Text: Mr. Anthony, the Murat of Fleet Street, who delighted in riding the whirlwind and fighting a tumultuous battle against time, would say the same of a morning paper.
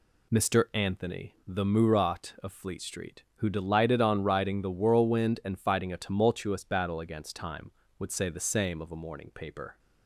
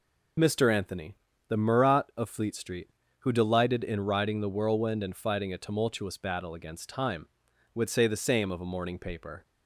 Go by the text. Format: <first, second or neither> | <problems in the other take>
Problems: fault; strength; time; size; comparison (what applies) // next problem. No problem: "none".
second | says "on" for "in"; at 3.9 s